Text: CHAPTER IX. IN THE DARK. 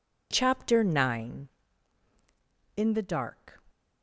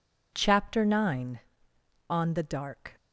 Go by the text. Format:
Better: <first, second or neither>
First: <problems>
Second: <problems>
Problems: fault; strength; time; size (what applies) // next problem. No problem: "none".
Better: first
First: none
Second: says "On" for "IN"; at 2.0 s